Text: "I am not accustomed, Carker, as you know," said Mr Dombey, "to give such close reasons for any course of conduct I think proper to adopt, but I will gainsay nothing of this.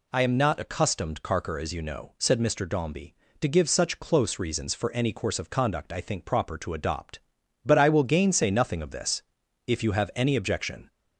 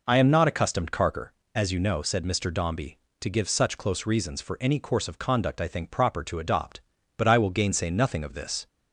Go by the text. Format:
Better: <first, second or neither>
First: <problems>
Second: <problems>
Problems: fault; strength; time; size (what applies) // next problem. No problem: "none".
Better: second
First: goes on to say "If you have any objection"; noticeable; from 9.6 s on; 1.2 s long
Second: none